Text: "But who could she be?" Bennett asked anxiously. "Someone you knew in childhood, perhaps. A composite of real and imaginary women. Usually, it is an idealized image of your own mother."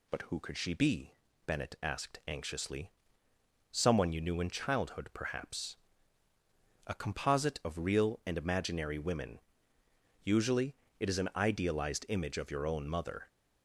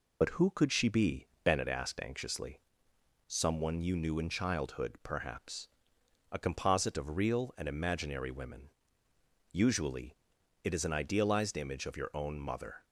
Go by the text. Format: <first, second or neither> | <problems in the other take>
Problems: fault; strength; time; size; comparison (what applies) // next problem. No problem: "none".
first | loses the start of "But"; at 0.2 s; 60 ms